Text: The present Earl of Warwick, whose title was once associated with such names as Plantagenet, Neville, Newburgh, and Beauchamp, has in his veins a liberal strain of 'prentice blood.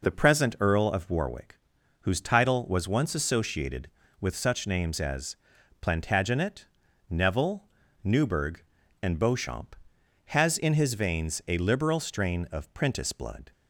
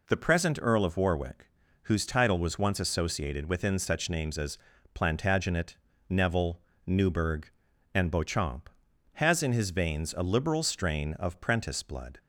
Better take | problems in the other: first | says "within" for "with"; at 3.4 s // pauses between "as" and "Plantagenet"; slight; at 4.5 s; 0.34 s long; also in the first

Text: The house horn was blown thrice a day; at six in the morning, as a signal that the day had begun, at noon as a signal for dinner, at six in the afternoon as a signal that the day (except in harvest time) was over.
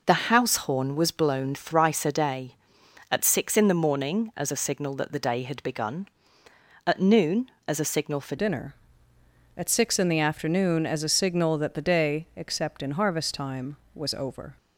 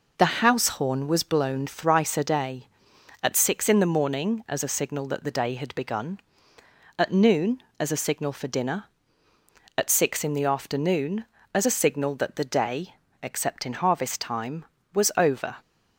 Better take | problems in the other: second | changes voice at "dinner"; from 8.3 s on; 6.2 s long

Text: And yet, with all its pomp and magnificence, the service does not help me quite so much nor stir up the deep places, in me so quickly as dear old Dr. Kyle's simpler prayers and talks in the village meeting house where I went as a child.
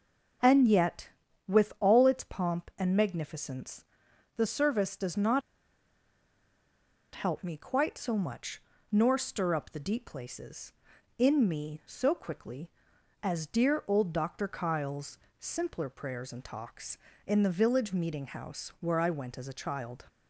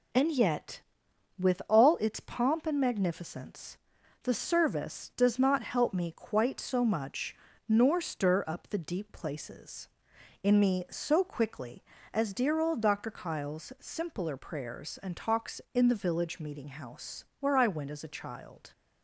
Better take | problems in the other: second | starts louder than the rest; until 1.8 s; 6 dB // pauses between "not" and "help"; strong; at 5.4 s; 1.7 s long // pauses between "much" and "nor"; slight; at 8.6 s; 0.30 s long; slight in the second // pauses between "Kyle's" and "simpler"; slight; at 15.1 s; 0.20 s long

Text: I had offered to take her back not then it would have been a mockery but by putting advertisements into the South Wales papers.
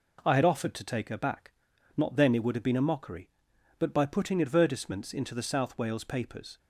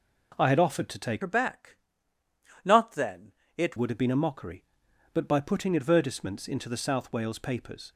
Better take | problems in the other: first | changes voice from "her" to "it"; from 1.2 to 3.7 s; 2.5 s long // pauses between "back" and "not"; noticeable; at 1.7 s; 0.86 s long; also in the first // pauses between "then" and "it"; slight; at 3.3 s; 0.24 s long

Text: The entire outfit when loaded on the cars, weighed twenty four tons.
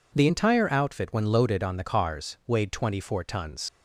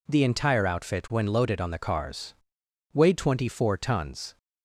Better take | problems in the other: second | leaves "tons" unfinished; at 3.6 s; 90 ms

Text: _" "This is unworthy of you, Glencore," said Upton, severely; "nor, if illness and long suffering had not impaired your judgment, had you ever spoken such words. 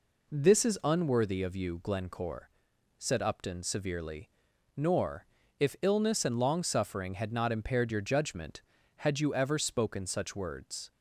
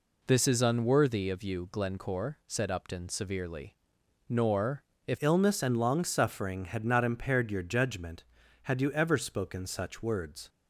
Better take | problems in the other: first | changes voice at "illness"; from 5.2 s on; 5.2 s long

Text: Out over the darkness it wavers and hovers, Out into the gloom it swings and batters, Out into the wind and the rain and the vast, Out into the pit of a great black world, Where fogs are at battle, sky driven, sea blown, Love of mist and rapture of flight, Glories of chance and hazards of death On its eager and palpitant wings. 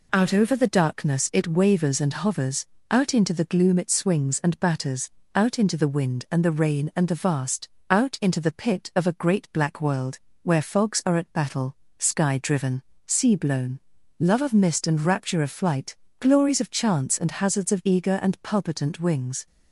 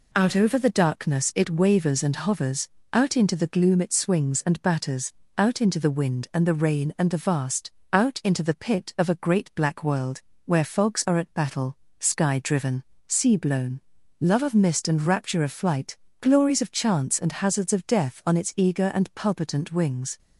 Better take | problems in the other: second | skips "death On its"; at 17.8 s

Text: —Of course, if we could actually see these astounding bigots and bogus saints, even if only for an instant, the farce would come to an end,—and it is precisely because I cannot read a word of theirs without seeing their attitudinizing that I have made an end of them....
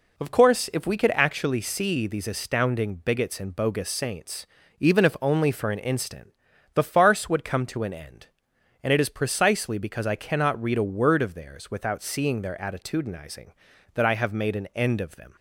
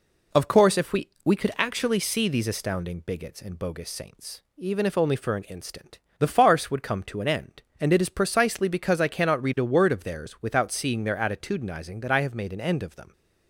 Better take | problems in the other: first | says "we" twice; at 1.2 s

